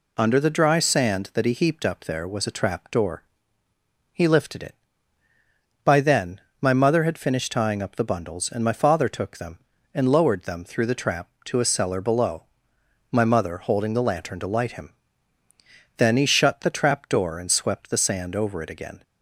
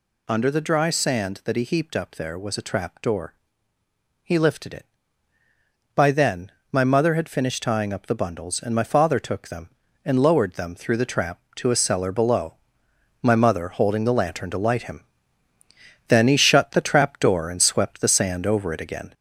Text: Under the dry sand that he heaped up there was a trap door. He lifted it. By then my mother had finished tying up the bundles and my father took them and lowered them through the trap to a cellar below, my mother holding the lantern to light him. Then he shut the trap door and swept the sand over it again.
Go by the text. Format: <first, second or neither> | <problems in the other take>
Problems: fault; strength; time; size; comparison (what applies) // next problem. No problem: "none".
first | gets louder; throughout; 3.5 dB // pauses between "then" and "my"; slight; at 6.4 s; 0.22 s long; slight in the first